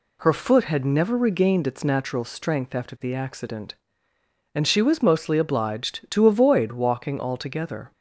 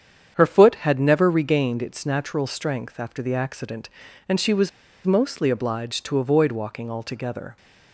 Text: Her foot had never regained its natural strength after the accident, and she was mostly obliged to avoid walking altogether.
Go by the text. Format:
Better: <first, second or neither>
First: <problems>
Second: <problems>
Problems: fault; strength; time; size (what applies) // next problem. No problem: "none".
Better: first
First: none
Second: starts louder than the rest; strong; until 1.3 s; 8 dB // pauses between "was" and "mostly"; at 4.6 s; 0.36 s long